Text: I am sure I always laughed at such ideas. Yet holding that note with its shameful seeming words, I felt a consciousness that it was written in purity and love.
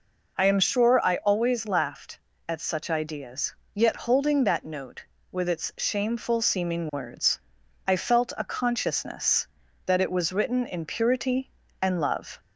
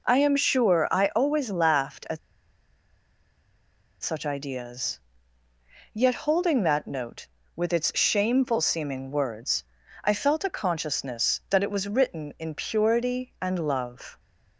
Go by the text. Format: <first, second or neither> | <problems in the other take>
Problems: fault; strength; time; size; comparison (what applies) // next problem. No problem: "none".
first | pauses between "at" and "such"; strong; at 2.1 s; 1.8 s long